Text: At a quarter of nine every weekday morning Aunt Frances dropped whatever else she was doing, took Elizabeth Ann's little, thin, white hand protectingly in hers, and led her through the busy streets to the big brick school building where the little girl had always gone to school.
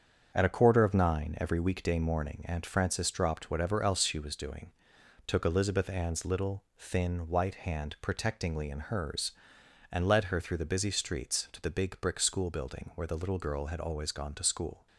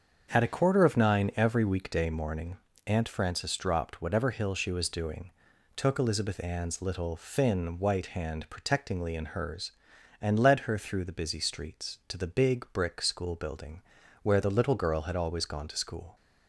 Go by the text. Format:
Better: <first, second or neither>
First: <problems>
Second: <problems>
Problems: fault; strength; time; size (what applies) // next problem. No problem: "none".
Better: first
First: starts louder than the rest; strong; until 1.3 s; 7 dB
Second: starts louder than the rest; until 1.3 s; 7 dB // pauses between "morning" and "Aunt"; slight; at 2.5 s; 0.28 s long // says "hill" for "else"; at 4.2 s // pauses between "building" and "where"; at 13.8 s; 0.40 s long